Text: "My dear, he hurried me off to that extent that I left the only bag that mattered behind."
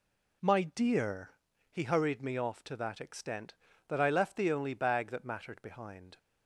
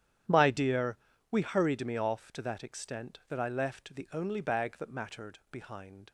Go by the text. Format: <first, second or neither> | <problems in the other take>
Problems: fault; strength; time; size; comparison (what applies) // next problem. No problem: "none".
first | starts louder than the rest; strong; until 1.6 s; 10.5 dB // says "we" for "he"; at 1.3 s